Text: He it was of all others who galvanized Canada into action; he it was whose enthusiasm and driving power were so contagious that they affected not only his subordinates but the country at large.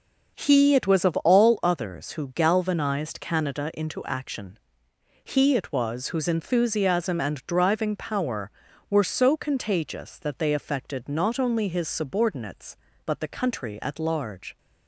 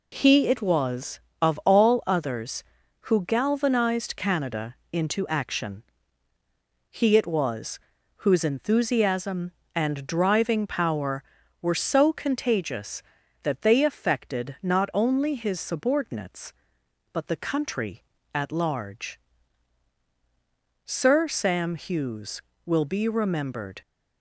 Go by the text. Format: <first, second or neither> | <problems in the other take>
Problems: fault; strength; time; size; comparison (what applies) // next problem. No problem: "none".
first | pauses between "Canada" and "into"; slight; at 4.7 s; 0.16 s long // pauses between "was" and "whose"; at 7.7 s; 0.38 s long // goes on to say "Sir Sam Hughes will be remembered"; strong; from 20.8 s on; 2.9 s long